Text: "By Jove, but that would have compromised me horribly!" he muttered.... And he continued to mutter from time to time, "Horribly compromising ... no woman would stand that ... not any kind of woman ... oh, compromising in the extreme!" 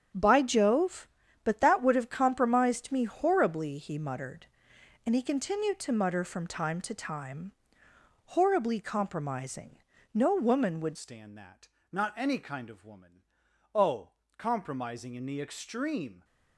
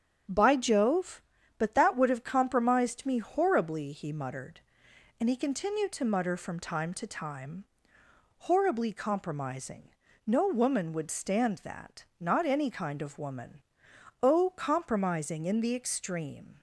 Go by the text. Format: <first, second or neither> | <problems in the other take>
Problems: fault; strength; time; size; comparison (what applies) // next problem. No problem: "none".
second | starts louder than the rest; strong; until 1.5 s; 8.5 dB; strong in the second // changes voice at "stand"; from 10.9 s on; 5.3 s long